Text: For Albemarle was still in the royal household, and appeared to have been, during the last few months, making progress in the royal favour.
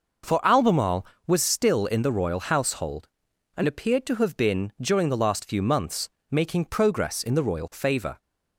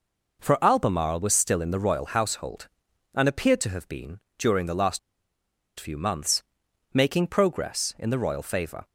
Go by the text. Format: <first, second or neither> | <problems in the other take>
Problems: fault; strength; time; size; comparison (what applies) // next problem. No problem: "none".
first | pauses between "last" and "few"; noticeable; at 4.9 s; 0.80 s long